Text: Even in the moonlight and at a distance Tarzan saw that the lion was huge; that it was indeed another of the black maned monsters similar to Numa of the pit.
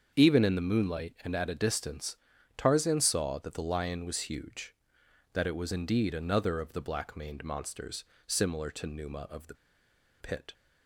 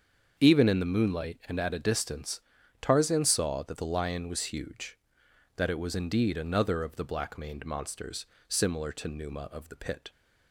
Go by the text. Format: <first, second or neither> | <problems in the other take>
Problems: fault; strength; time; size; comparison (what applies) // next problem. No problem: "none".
second | starts louder than the rest; until 1.1 s; 6.5 dB; also in the second // pauses between "distance" and "Tarzan"; at 2.1 s; 0.38 s long; also in the second // pauses between "monsters" and "similar"; slight; at 8.0 s; 0.22 s long; slight in the second // pauses between "the" and "pit"; noticeable; at 9.5 s; 0.65 s long